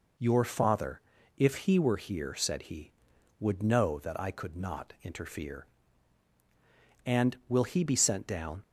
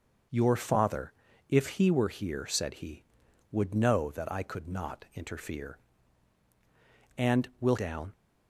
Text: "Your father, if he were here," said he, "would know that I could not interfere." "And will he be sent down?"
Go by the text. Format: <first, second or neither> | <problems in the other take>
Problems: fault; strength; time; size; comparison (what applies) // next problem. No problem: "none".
first | starts louder than the rest; noticeable; until 1.6 s; 6 dB // skips "he be sent"; at 7.7 s